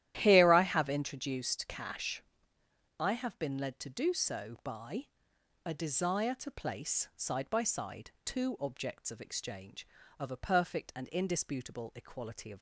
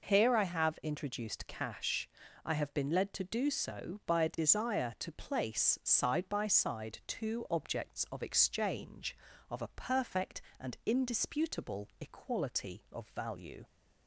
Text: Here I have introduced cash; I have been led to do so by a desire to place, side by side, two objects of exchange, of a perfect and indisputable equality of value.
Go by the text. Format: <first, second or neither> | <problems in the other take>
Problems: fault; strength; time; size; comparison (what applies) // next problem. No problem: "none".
second | starts louder than the rest; strong; until 1.1 s; 12.5 dB // pauses between "by" and "a"; noticeable; at 5.0 s; 0.58 s long // stops before "value"; at 12.5 s